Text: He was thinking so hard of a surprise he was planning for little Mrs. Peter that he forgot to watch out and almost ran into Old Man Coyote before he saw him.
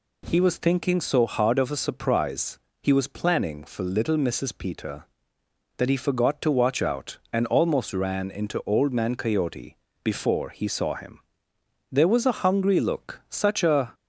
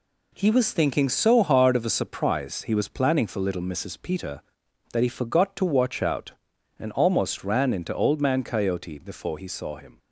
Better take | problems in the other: second | pauses between "surprise" and "he"; slight; at 2.5 s; 0.24 s long // pauses between "Coyote" and "before"; slight; at 9.7 s; 0.24 s long // goes on to say "There was a hungry look such a"; strong; from 11.9 s on; 2.0 s long

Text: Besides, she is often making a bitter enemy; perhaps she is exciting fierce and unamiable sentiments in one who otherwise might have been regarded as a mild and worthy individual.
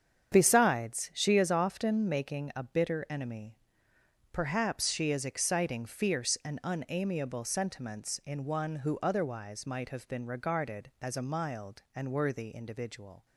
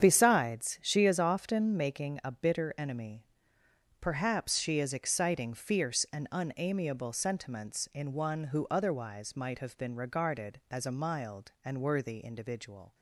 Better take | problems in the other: neither | starts louder than the rest; strong; the same in both

